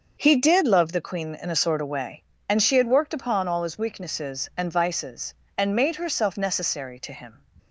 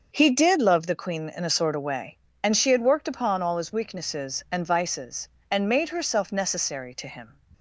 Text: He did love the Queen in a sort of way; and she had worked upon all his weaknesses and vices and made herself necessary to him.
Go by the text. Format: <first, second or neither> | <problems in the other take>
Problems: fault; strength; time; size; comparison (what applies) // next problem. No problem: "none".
neither | starts louder than the rest; the same in both